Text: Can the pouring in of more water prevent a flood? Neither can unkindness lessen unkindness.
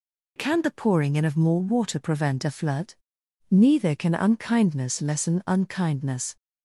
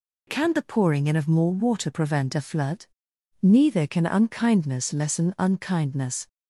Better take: neither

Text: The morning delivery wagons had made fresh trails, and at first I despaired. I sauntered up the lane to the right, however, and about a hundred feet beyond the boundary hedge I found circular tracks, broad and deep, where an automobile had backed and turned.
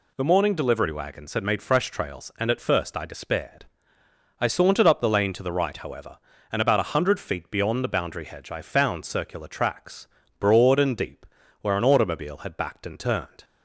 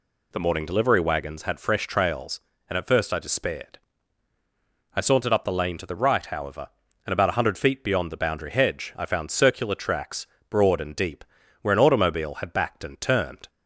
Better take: first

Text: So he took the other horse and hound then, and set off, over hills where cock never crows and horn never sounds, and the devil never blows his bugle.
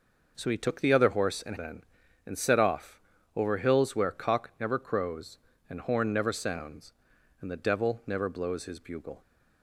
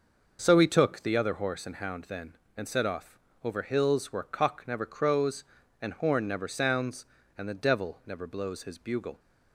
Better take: second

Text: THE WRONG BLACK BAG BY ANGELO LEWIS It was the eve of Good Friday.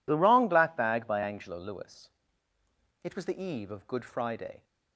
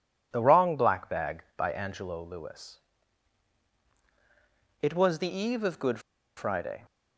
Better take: first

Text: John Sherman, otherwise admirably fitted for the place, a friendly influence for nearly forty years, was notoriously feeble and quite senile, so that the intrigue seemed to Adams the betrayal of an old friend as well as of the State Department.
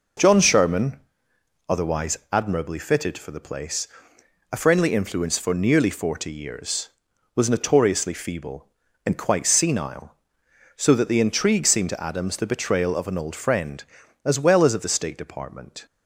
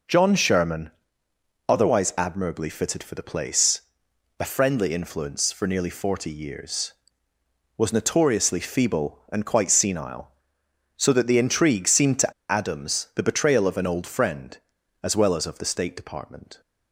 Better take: first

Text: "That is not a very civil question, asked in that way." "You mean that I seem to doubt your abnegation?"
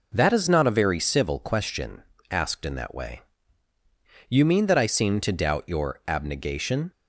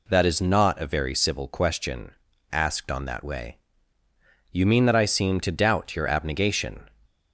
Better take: first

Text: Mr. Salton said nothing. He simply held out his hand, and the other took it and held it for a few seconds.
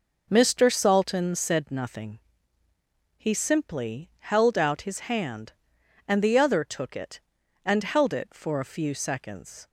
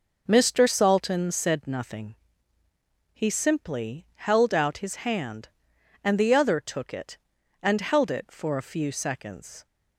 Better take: neither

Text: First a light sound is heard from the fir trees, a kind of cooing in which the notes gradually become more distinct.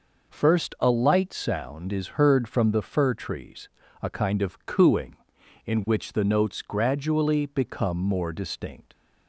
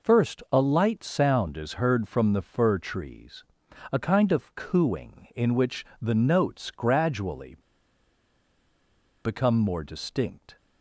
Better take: first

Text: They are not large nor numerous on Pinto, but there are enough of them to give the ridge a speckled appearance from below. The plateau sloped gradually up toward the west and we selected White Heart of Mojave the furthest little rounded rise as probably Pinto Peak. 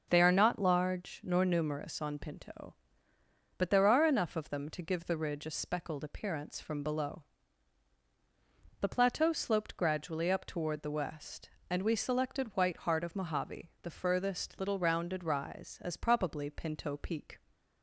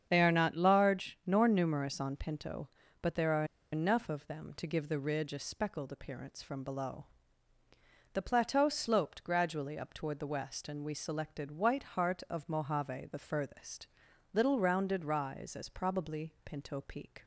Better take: first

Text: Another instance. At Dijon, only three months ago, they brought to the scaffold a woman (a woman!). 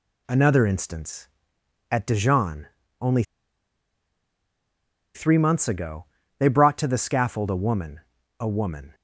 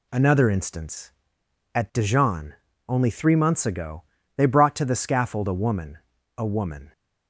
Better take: second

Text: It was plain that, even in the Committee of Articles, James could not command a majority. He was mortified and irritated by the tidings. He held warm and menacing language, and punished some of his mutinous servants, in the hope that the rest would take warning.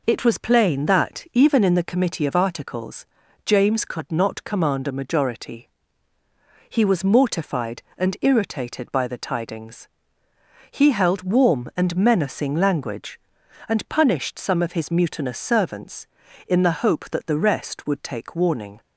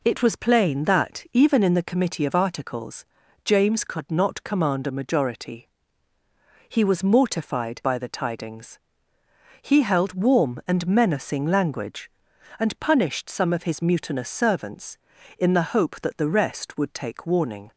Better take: first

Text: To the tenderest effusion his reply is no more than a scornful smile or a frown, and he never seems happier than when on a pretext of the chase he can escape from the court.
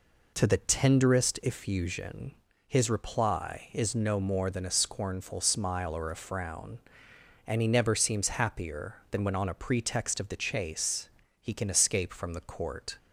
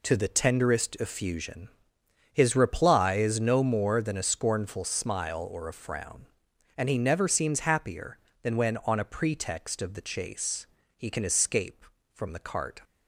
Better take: first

